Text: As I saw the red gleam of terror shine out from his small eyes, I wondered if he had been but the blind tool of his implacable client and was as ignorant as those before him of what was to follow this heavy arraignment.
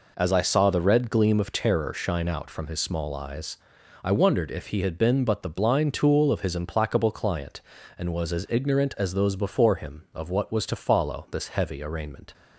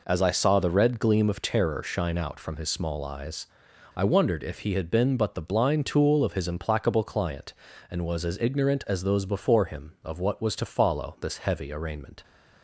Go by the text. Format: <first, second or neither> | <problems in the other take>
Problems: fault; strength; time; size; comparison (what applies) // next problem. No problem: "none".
neither | none